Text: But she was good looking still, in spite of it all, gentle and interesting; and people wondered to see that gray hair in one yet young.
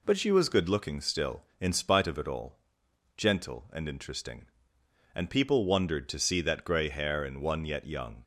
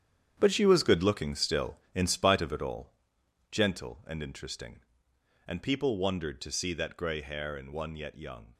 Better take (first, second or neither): first